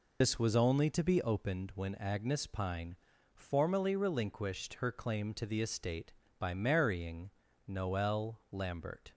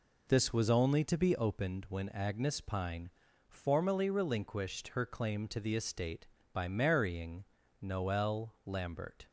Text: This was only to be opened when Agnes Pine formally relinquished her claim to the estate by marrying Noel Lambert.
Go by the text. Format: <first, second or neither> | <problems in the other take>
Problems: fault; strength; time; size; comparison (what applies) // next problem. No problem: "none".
second | loses the start of "This"; at 0.2 s; 60 ms // pauses between "Pine" and "formally"; at 2.9 s; 0.40 s long; also in the second // pauses between "marrying" and "Noel"; slight; at 7.3 s; 0.36 s long; slight in the second